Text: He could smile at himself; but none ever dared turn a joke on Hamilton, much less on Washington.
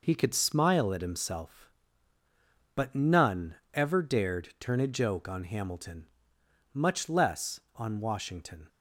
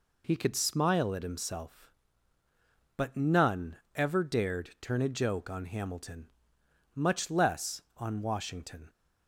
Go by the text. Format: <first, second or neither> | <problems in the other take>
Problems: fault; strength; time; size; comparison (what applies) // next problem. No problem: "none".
second | gets quieter; throughout; 6 dB // pauses between "none" and "ever"; slight; at 3.5 s; 0.18 s long; slight in the second